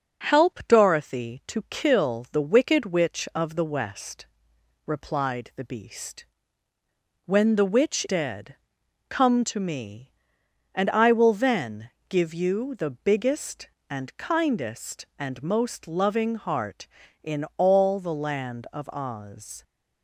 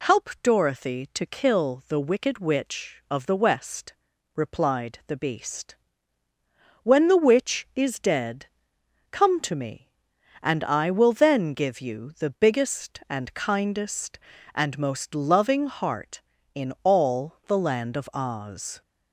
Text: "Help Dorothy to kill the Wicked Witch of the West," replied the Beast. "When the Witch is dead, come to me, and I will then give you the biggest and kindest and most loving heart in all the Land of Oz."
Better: second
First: skips "is"; at 8.0 s // pauses between "then" and "give"; slight; at 11.9 s; 0.18 s long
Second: none

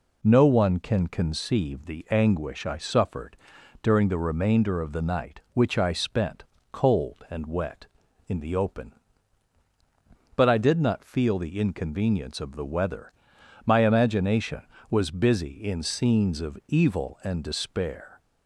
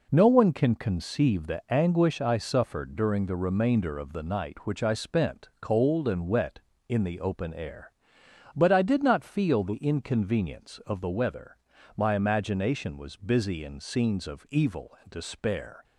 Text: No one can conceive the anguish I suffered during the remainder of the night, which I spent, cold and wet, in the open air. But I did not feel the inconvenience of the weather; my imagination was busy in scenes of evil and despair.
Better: second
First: pauses between "suffered" and "during"; noticeable; at 3.3 s; 0.46 s long // skips "air"; at 9.6 s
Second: none

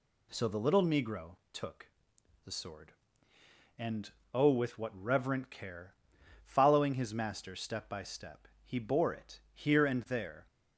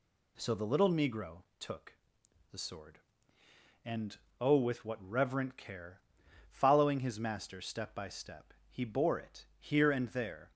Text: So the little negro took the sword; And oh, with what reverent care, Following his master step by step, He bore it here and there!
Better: neither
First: pauses between "negro" and "took"; slight; at 1.3 s; 0.16 s long // pauses between "took" and "the"; noticeable; at 1.8 s; 0.58 s long // pauses between "And" and "oh"; slight; at 4.1 s; 0.20 s long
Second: pauses between "negro" and "took"; slight; at 1.4 s; 0.16 s long // pauses between "took" and "the"; noticeable; at 1.9 s; 0.58 s long // pauses between "And" and "oh"; slight; at 4.1 s; 0.20 s long

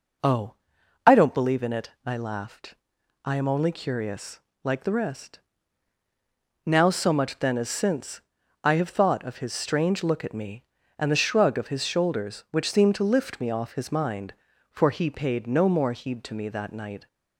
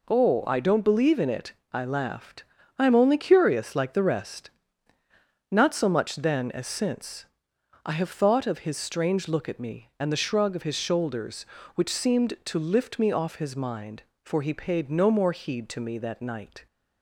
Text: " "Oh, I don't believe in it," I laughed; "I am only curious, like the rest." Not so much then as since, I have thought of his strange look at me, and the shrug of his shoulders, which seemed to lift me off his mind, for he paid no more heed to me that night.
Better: second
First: says "Now" for "Not"; at 6.6 s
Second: none

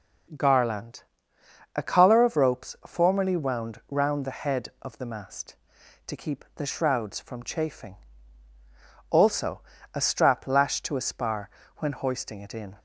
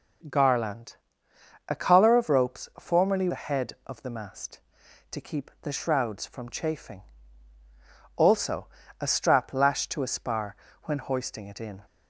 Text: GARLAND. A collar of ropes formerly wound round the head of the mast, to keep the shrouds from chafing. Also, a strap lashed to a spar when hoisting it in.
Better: first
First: pauses between "spar" and "when"; slight; at 11.4 s; 0.28 s long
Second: skips "wound round"; at 3.2 s // pauses between "spar" and "when"; slight; at 10.5 s; 0.28 s long

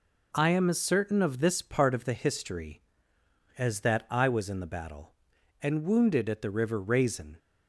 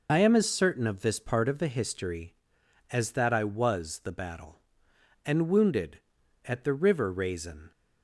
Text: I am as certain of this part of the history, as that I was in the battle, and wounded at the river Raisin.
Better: first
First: none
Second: skips "in"; at 4.0 s

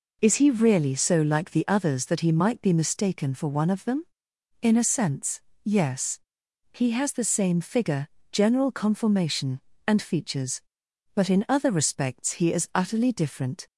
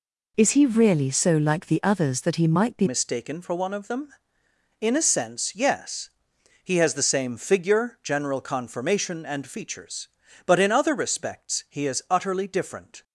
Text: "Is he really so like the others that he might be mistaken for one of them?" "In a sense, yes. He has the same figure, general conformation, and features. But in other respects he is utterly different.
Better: first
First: none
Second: changes voice at "mistaken"; from 2.8 s on; 10.2 s long

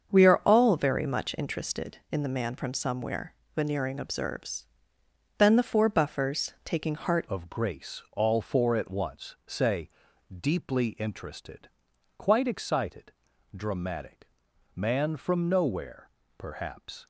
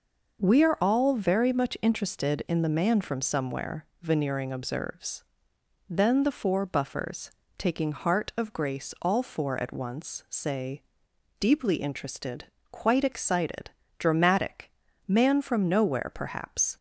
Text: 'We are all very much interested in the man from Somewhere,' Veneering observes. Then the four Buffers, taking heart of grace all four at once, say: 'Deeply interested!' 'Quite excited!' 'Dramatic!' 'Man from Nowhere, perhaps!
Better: second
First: starts louder than the rest; strong; until 1.1 s; 7 dB // changes voice at "of"; from 7.2 s on; 9.8 s long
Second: none

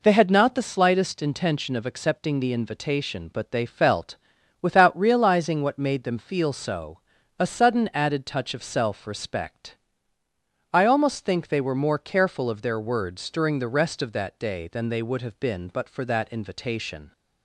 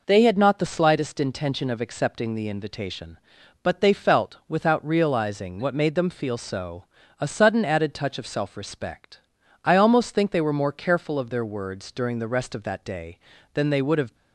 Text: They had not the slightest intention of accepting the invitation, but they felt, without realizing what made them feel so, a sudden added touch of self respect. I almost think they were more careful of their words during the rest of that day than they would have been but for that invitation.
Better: first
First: none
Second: stops before "been but for that invitation"; at 14.1 s

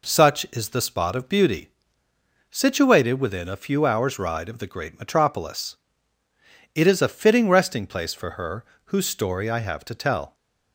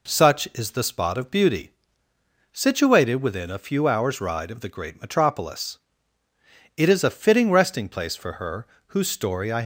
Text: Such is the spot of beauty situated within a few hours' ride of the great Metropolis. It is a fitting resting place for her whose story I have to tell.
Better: first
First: pauses between "beauty" and "situated"; noticeable; at 1.7 s; 0.80 s long // pauses between "her" and "whose"; slight; at 8.6 s; 0.20 s long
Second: pauses between "beauty" and "situated"; noticeable; at 1.7 s; 0.80 s long // pauses between "her" and "whose"; slight; at 8.6 s; 0.20 s long // stops before "have to tell"; at 9.6 s

